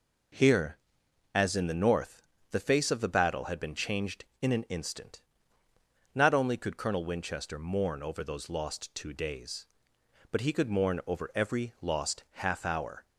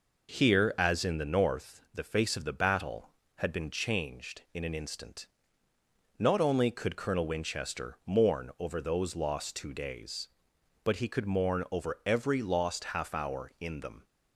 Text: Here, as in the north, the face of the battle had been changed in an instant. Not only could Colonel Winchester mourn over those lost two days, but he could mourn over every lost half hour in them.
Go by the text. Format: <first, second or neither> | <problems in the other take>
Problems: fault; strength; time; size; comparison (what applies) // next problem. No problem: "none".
second | stops before "in them"; at 13.0 s